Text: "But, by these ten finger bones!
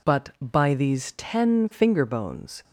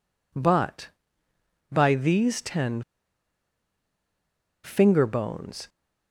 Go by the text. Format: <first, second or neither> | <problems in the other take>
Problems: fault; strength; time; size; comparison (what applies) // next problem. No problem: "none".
first | pauses between "ten" and "finger"; strong; at 2.8 s; 1.8 s long